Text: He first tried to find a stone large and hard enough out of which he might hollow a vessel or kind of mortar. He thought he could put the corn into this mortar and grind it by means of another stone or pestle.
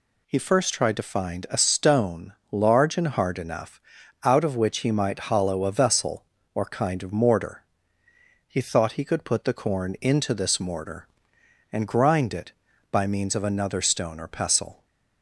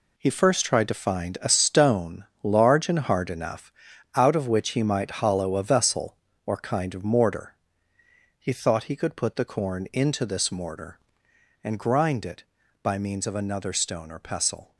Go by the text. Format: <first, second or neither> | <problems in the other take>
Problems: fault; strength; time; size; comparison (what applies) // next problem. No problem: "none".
first | gets quieter; strong; throughout; 9 dB // pauses between "stone" and "large"; slight; at 2.2 s; 0.18 s long; slight in the first // pauses between "enough" and "out"; at 3.7 s; 0.42 s long; also in the first